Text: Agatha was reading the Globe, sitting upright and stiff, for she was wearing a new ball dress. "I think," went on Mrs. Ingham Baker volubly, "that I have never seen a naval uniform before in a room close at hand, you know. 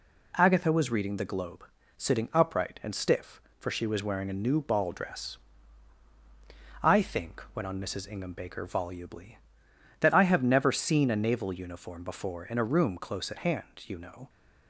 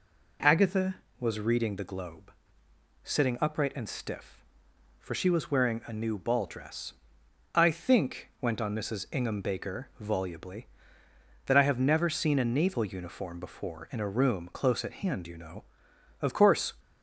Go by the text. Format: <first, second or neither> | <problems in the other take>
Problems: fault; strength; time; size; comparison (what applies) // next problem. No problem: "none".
first | goes on to say "Of course"; from 16.2 s on; 0.54 s long